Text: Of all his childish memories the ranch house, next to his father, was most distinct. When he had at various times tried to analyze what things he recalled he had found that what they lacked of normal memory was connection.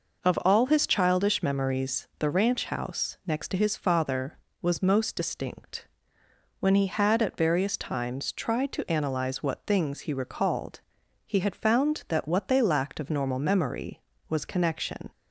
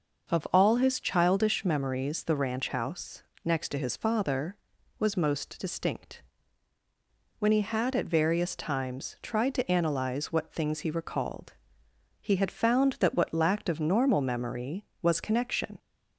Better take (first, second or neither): first